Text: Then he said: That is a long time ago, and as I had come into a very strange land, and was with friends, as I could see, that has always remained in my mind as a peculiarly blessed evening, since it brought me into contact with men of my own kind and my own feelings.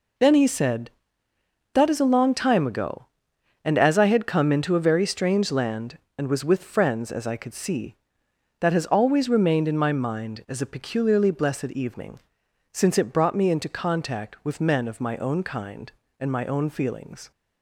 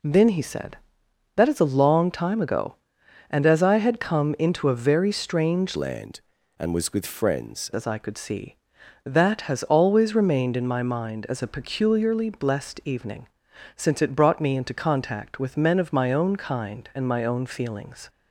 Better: first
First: none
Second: changes voice from "land" to "friends"; from 5.7 to 7.7 s; 2.0 s long

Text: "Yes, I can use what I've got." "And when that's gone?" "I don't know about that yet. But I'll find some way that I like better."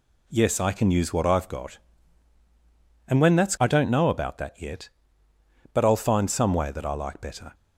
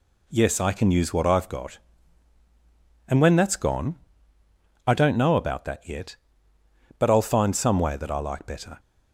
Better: second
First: skips "gone"; at 3.5 s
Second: none

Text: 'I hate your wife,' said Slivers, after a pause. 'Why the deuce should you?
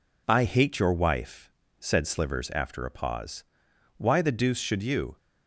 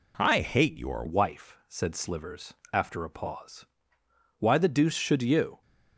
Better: first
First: none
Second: changes voice at "wife"; from 1.0 s on; 4.6 s long

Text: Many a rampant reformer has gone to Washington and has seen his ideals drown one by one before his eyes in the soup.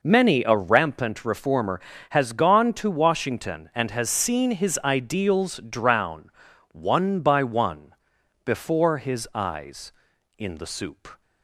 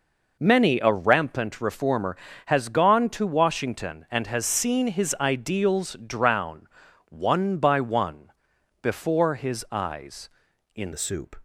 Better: first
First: pauses between "drown" and "one"; at 6.3 s; 0.42 s long // pauses between "one" and "before"; noticeable; at 7.9 s; 0.52 s long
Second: pauses between "drown" and "one"; at 6.6 s; 0.42 s long // pauses between "one" and "before"; noticeable; at 8.3 s; 0.52 s long // changes voice at "the"; from 10.9 s on; 0.4 s long

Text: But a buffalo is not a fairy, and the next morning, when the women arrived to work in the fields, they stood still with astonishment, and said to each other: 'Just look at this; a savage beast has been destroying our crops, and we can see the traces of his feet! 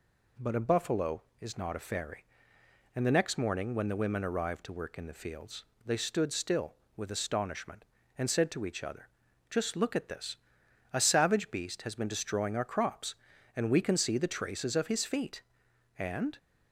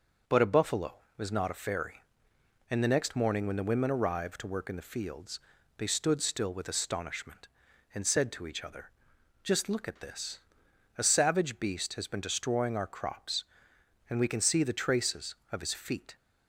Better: second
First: goes on to say "And"; slight; from 15.9 s on; 0.40 s long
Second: none

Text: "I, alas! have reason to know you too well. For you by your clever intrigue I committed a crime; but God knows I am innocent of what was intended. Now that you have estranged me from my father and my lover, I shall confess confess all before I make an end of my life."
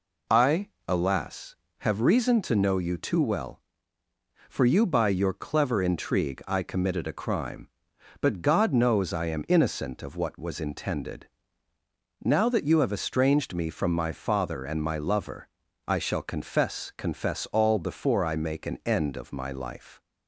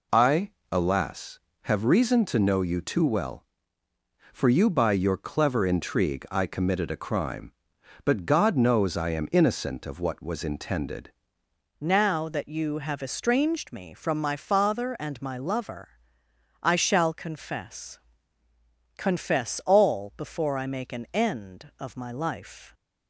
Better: first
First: none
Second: changes voice at "Now"; from 11.7 s on; 11.0 s long // pauses between "confess" and "confess"; noticeable; at 17.9 s; 0.98 s long

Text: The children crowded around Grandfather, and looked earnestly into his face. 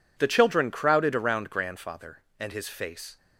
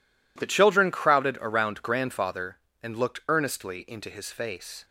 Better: second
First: skips "looked earnestly into"; at 2.5 s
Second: none

